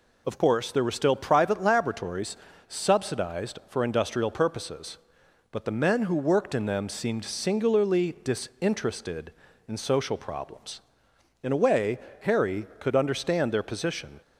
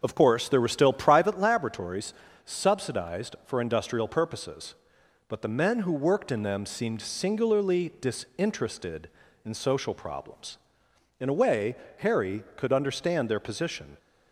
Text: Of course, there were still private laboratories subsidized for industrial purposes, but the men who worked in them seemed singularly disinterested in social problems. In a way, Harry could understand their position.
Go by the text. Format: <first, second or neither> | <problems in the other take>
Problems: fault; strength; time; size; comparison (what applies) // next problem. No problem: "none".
first | starts louder than the rest; until 1.3 s; 6 dB // pauses between "laboratories" and "subsidized"; slight; at 2.1 s; 0.30 s long; slight in the first